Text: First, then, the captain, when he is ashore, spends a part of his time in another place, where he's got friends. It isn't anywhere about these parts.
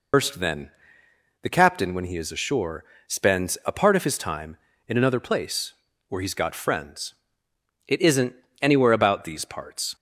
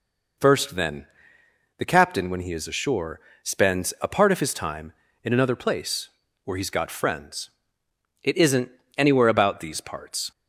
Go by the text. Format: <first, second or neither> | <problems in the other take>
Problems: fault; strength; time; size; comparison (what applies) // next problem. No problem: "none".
second | loses the start of "First"; at 0.1 s; 105 ms // pauses between "isn't" and "anywhere"; slight; at 8.3 s; 0.26 s long; slight in the second